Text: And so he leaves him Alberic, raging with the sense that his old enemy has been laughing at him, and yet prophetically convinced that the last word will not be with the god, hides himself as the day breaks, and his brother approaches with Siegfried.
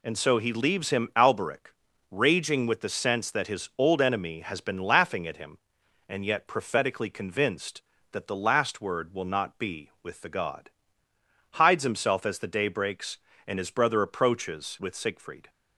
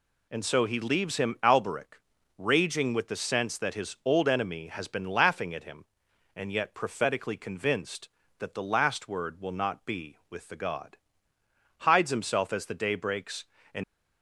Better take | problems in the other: first | stops before "his brother approaches with Siegfried"; at 13.8 s

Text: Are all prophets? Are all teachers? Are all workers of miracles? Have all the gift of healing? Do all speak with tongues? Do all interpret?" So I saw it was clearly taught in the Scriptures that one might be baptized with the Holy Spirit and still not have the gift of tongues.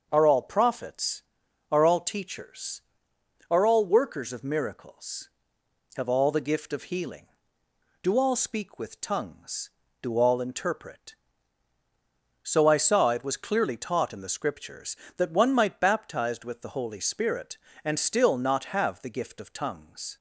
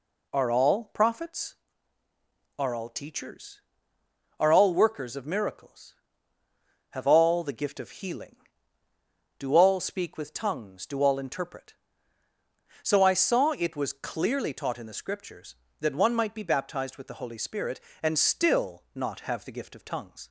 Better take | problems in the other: second | starts louder than the rest; until 1.1 s; 6.5 dB // skips "be"; at 15.8 s

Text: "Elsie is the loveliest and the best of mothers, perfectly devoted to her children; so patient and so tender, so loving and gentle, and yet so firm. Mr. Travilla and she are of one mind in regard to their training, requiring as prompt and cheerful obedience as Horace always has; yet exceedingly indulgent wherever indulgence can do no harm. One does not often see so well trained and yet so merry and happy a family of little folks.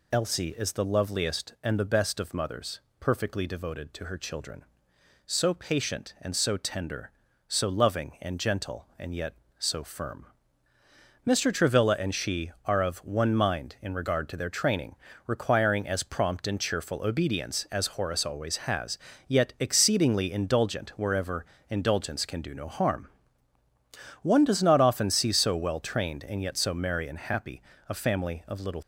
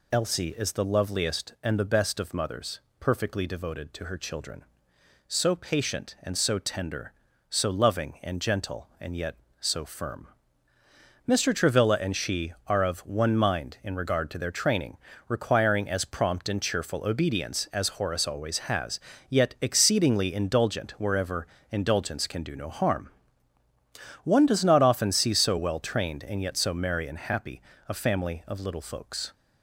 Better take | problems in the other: second | pauses between "wherever" and "indulgence"; slight; at 21.4 s; 0.24 s long; slight in the second // pauses between "happy" and "a"; slight; at 27.6 s; 0.26 s long; slight in the second // stops before "folks"; at 28.8 s

